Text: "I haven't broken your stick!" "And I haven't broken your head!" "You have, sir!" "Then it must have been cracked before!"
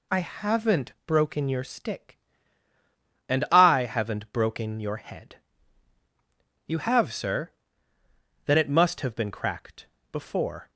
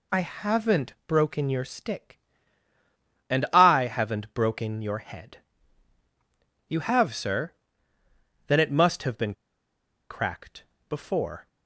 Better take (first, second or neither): first